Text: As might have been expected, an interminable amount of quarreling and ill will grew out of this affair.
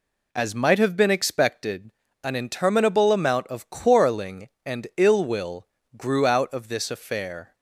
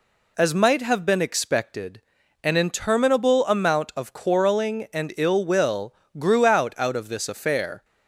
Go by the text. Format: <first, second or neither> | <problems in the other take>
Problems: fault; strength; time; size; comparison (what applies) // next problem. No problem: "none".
first | pauses between "will" and "grew"; slight; at 5.9 s; 0.24 s long; slight in the first // says "out" twice; at 6.7 s